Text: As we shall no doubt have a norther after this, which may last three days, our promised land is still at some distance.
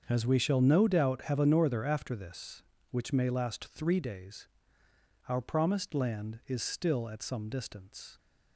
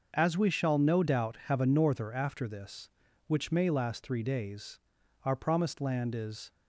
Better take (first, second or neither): first